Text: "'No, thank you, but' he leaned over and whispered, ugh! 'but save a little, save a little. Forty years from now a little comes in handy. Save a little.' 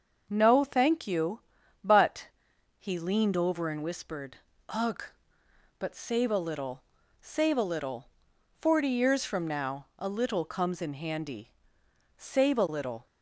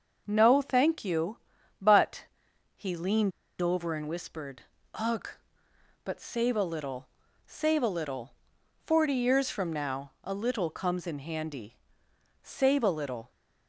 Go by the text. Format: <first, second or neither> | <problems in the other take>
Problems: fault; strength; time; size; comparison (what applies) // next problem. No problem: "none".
first | starts louder than the rest; noticeable; until 1.2 s; 6 dB; noticeable in the first // pauses between "but" and "he"; noticeable; at 2.2 s; 0.52 s long; noticeable in the first // pauses between "leaned" and "over"; slight; at 3.3 s; 0.30 s long